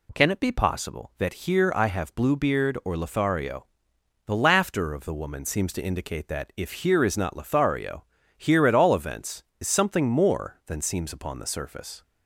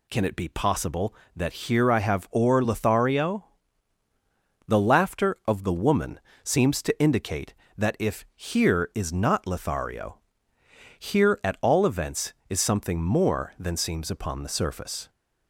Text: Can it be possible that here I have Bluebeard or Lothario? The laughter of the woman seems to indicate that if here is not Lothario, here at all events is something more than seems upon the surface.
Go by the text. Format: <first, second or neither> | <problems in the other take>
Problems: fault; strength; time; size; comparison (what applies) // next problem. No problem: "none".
first | skips "Bluebeard"; at 2.2 s // pauses between "woman" and "seems"; slight; at 6.2 s; 0.24 s long